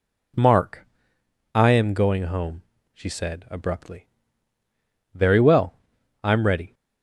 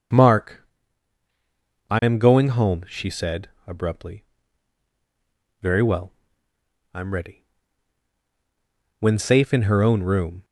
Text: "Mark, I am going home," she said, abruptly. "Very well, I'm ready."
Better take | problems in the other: first | starts louder than the rest; until 2.4 s; 6.5 dB // goes on to say "When safe in her own room"; from 9.0 s on; 1.4 s long

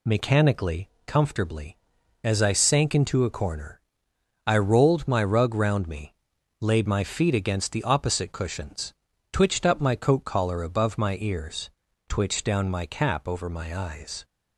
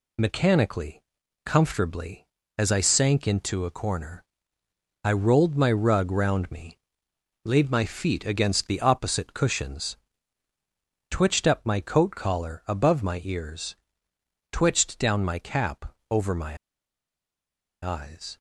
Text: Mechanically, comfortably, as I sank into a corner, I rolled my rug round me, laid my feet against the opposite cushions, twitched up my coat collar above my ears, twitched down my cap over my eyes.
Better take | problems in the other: first | pauses between "cap" and "over"; slight; at 15.9 s; 0.16 s long // pauses between "my" and "eyes"; strong; at 16.5 s; 1.2 s long

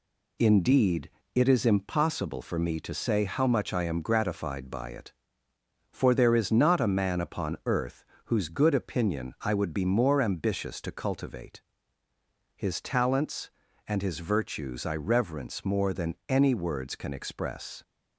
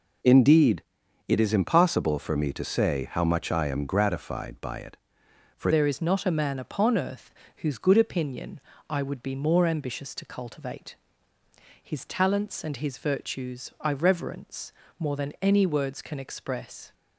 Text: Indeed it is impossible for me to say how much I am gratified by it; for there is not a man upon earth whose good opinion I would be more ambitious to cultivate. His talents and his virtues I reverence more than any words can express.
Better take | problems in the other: first | pauses between "Indeed" and "it"; at 0.8 s; 0.44 s long; slight in the first // changes voice at "there"; from 5.7 s on; 11.2 s long // pauses between "earth" and "whose"; slight; at 7.3 s; 0.24 s long; slight in the first // pauses between "opinion" and "I"; slight; at 8.6 s; 0.28 s long // pauses between "reverence" and "more"; slight; at 14.7 s; 0.28 s long

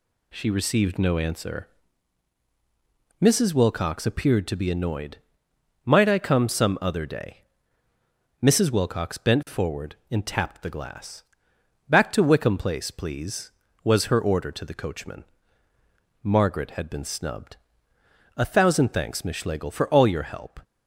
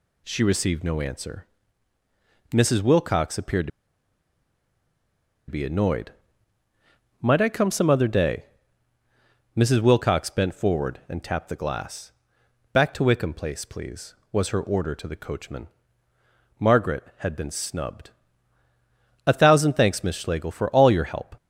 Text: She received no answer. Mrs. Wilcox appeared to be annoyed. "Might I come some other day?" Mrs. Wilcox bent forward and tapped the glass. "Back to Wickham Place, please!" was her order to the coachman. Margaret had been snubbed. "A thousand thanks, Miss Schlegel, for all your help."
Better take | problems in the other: first | pauses between "to" and "be"; strong; at 3.7 s; 1.8 s long

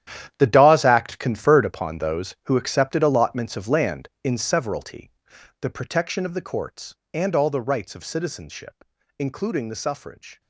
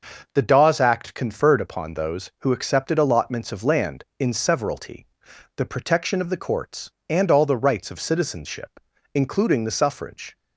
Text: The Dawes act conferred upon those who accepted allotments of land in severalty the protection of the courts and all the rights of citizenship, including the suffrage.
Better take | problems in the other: second | gets quieter; strong; throughout; 15.5 dB // starts louder than the rest; strong; until 1.3 s; 11 dB; noticeable in the second // pauses between "severalty" and "the"; noticeable; at 5.0 s; 0.50 s long; noticeable in the second

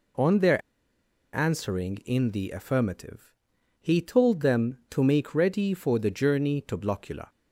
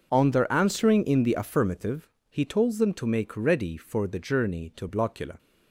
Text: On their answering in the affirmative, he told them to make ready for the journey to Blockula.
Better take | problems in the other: second | pauses between "their" and "answering"; noticeable; at 0.6 s; 0.73 s long

